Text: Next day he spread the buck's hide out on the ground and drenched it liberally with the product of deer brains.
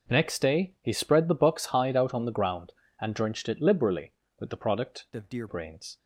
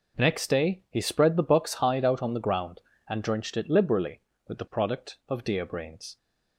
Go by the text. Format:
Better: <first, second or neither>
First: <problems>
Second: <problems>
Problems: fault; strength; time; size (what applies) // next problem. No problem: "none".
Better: second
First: changes voice from "of" to "deer"; from 5.1 to 5.4 s; 0.3 s long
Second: none